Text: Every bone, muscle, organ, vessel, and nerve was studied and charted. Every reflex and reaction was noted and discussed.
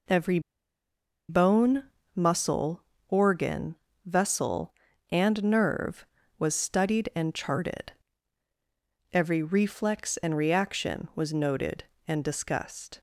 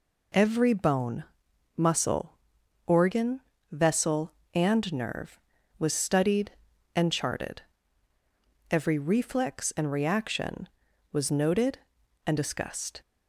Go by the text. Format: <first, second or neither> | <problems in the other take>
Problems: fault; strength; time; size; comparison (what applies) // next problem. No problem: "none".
second | pauses between "Every" and "bone"; noticeable; at 0.3 s; 0.89 s long